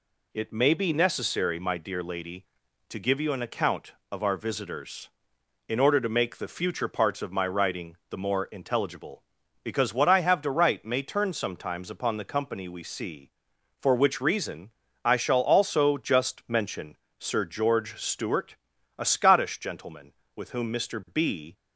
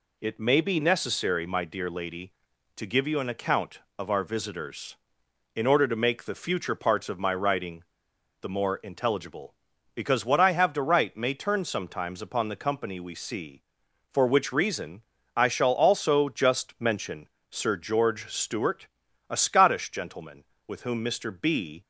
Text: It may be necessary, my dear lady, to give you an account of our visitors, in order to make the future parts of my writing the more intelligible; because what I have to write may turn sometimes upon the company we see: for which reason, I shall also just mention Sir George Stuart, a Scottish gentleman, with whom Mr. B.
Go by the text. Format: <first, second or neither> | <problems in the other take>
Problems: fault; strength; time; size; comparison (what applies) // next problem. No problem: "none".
first | pauses between "writing" and "the"; noticeable; at 7.8 s; 0.58 s long // pauses between "mention" and "Sir"; slight; at 17.2 s; 0.22 s long; slight in the first